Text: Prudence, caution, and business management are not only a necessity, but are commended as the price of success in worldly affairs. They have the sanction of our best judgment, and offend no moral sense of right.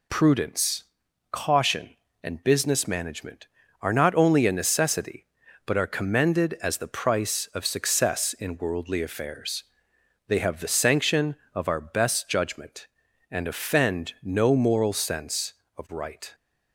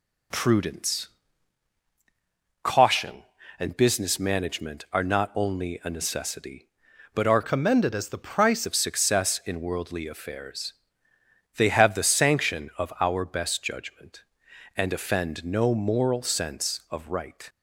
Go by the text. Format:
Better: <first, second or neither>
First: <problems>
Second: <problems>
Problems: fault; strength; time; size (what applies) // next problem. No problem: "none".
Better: first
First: none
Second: changes voice from "commended" to "price"; from 7.4 to 8.6 s; 1.2 s long